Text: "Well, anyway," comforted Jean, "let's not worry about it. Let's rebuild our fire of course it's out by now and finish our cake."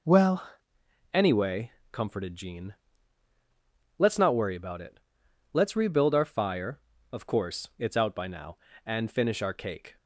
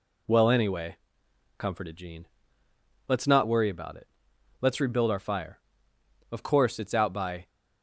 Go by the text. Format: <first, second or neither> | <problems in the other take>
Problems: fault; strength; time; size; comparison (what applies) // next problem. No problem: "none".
first | stops before "now and finish our cake"; at 7.4 s